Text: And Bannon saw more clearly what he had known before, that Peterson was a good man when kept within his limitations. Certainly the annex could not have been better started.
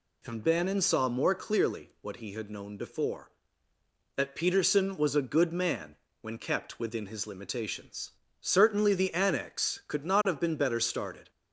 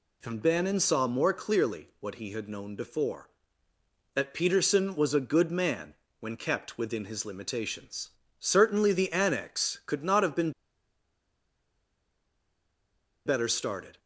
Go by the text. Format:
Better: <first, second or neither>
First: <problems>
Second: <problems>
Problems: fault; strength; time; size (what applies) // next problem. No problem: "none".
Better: first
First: pauses between "man" and "when"; slight; at 5.9 s; 0.26 s long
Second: pauses between "man" and "when"; slight; at 5.9 s; 0.26 s long // pauses between "been" and "better"; strong; at 10.5 s; 2.7 s long